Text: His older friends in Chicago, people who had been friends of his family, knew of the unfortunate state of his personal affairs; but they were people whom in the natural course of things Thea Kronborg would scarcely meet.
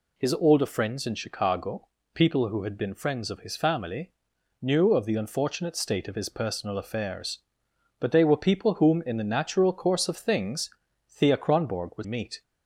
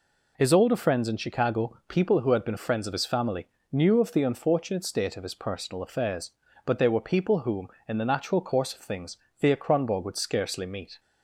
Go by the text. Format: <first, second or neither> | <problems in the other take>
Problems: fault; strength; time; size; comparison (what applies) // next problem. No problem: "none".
second | pauses between "things" and "Thea"; at 10.7 s; 0.40 s long; slight in the second // skips "scarcely"; at 12.0 s